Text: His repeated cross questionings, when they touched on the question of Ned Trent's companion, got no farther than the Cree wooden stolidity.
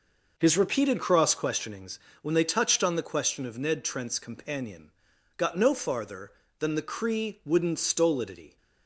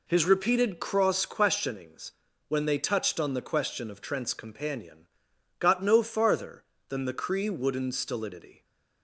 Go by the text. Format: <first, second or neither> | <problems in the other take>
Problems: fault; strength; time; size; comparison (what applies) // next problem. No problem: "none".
first | skips "Ned"; at 3.9 s // stays silent after the last word; slight; from 8.5 s on; 0.5 s long